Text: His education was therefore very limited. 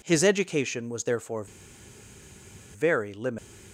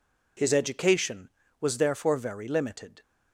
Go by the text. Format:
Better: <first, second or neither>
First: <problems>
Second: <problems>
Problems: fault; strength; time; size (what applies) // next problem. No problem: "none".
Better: second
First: pauses between "therefore" and "very"; strong; at 1.4 s; 1.3 s long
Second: none